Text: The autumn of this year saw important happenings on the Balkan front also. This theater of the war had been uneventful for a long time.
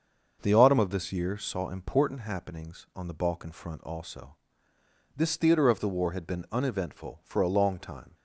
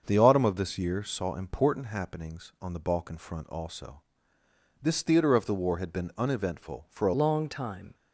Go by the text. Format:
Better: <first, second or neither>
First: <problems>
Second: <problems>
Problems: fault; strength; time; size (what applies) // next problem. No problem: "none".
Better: first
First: starts louder than the rest; until 1.4 s; 6.5 dB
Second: starts louder than the rest; until 1.0 s; 6.5 dB // changes voice at "long"; from 7.1 s on; 0.8 s long